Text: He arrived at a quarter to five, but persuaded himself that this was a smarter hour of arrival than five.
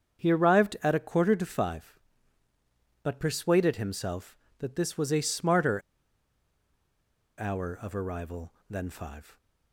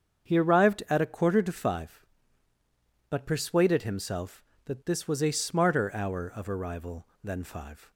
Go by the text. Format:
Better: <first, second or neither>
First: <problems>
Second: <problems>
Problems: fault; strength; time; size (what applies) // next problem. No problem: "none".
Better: second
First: starts louder than the rest; strong; until 1.2 s; 7 dB // pauses between "smarter" and "hour"; strong; at 5.7 s; 1.5 s long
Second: starts louder than the rest; strong; until 1.3 s; 7 dB